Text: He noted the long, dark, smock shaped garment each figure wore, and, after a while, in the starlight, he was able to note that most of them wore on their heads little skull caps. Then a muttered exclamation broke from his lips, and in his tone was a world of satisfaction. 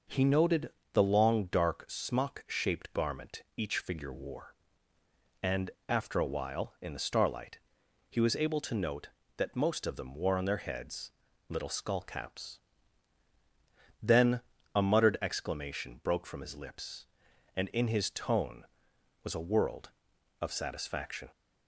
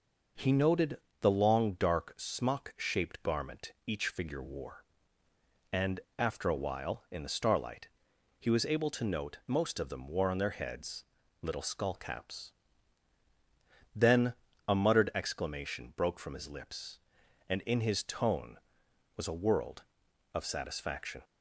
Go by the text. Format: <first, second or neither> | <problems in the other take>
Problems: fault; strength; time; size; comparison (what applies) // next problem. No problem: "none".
first | pauses between "noted" and "the"; slight; at 0.9 s; 0.24 s long; slight in the first // skips "that"; at 9.4 s // pauses between "heads" and "little"; at 11.0 s; 0.38 s long; also in the first // pauses between "Then" and "a"; slight; at 14.3 s; 0.34 s long; slight in the first